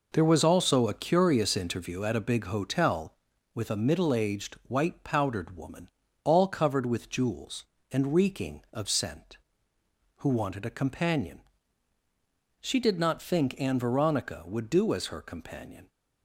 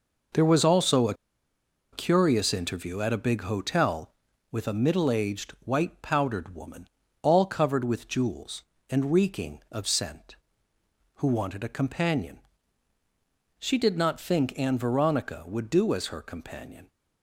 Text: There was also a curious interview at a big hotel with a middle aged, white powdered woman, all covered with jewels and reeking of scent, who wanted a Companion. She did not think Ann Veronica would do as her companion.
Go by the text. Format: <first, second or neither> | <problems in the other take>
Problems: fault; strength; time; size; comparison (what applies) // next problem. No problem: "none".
first | pauses between "a" and "curious"; noticeable; at 1.1 s; 0.78 s long